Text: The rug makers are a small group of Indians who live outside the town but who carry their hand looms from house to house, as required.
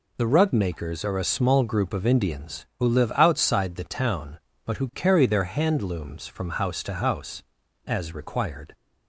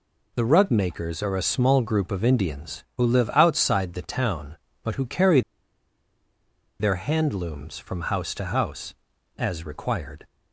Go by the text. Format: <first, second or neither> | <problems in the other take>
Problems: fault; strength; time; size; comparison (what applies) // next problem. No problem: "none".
first | pauses between "carry" and "their"; strong; at 5.4 s; 1.3 s long